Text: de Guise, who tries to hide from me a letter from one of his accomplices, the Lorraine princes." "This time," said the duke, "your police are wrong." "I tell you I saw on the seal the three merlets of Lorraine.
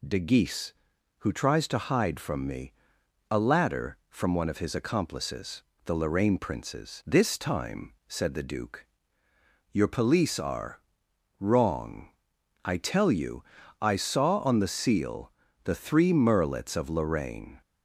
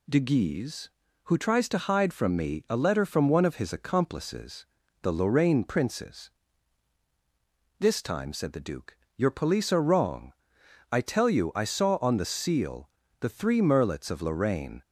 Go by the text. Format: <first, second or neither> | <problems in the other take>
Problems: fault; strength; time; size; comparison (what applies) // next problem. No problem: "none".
second | pauses between "me" and "a"; noticeable; at 2.7 s; 0.58 s long // says "ladder" for "letter"; at 3.3 s // pauses between "are" and "wrong"; noticeable; at 10.8 s; 0.58 s long // pauses between "you" and "I"; slight; at 13.4 s; 0.34 s long // pauses between "seal" and "the"; slight; at 15.3 s; 0.34 s long; slight in the second